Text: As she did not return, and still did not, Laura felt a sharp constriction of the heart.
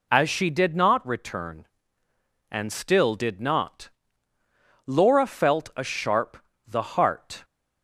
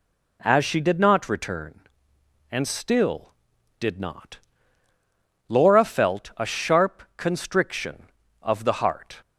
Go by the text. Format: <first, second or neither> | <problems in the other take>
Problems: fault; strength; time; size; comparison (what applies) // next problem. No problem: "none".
second | skips "constriction of"; at 6.5 s